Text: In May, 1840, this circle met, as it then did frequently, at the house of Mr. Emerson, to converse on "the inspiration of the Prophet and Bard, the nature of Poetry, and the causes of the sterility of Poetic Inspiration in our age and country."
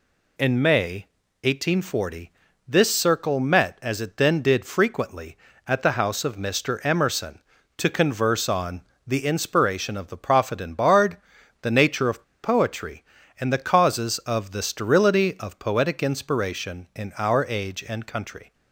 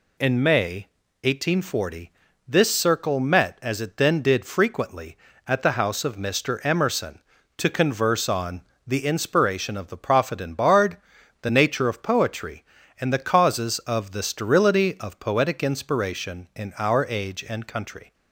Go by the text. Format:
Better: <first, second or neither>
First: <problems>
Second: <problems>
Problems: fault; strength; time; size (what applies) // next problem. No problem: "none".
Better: second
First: pauses between "on" and "the"; slight; at 8.8 s; 0.24 s long // pauses between "of" and "Poetry"; slight; at 12.2 s; 0.20 s long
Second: pauses between "on" and "the"; slight; at 8.6 s; 0.24 s long